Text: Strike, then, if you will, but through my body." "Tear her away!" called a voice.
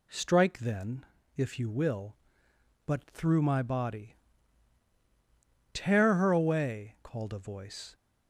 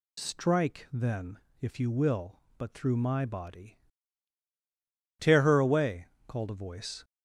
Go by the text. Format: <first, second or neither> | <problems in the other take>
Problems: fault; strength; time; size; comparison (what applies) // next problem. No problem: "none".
first | loses the start of "Strike"; at 0.1 s; 85 ms